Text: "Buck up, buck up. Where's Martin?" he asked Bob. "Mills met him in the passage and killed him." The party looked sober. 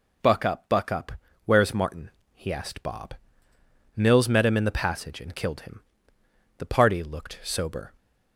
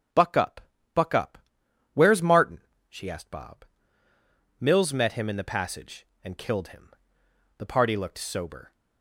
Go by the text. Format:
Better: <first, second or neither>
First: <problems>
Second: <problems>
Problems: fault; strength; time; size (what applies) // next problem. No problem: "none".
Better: first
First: none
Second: starts louder than the rest; strong; until 2.0 s; 7.5 dB // says "she" for "he"; at 2.8 s